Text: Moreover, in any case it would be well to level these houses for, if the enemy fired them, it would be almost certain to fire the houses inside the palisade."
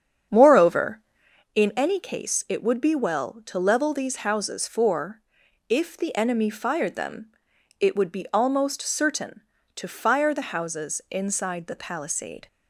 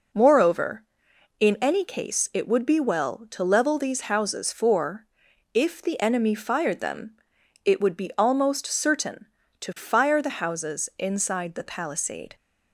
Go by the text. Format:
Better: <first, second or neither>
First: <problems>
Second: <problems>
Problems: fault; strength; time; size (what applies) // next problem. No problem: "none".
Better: second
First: starts louder than the rest; strong; until 1.5 s; 8 dB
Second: none